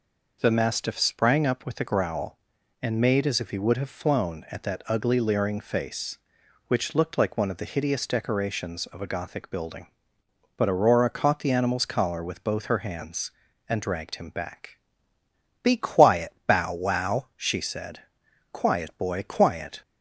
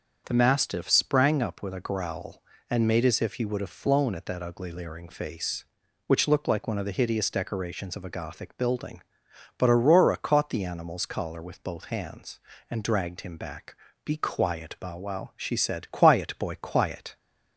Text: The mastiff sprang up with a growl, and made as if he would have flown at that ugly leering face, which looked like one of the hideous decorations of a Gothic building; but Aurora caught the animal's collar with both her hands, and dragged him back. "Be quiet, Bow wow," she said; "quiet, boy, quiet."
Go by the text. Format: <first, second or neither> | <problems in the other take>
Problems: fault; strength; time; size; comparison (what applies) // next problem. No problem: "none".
first | starts louder than the rest; until 1.2 s; 7 dB // skips "her"; at 11.9 s